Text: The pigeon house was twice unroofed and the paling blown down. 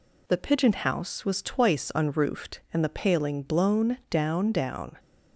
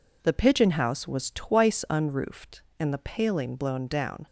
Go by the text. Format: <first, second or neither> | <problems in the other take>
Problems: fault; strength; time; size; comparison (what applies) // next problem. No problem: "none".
second | says "down" twice; at 4.5 s